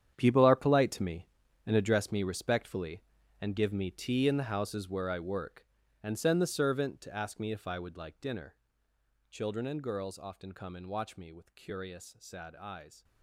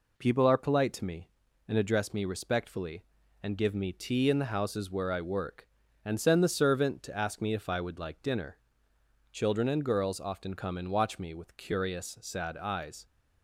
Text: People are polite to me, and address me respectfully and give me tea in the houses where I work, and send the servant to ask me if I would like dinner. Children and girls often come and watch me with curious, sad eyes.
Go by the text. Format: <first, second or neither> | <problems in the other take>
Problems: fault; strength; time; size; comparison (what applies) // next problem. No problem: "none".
second | gets quieter; strong; throughout; 14 dB